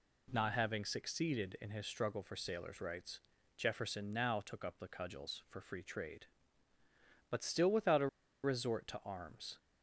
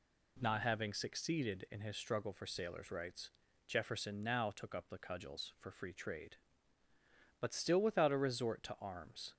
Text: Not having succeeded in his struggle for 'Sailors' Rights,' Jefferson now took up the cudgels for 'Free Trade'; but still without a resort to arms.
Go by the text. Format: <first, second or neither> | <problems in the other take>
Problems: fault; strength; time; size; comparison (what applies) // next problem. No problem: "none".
second | pauses between "a" and "resort"; at 8.0 s; 0.36 s long